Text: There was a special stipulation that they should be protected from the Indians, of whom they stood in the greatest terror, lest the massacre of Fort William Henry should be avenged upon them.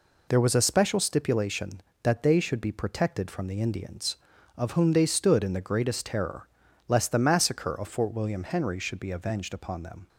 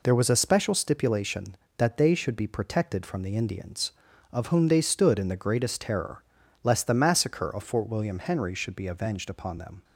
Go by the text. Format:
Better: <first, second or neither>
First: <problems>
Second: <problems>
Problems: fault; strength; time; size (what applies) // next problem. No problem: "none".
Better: neither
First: none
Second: none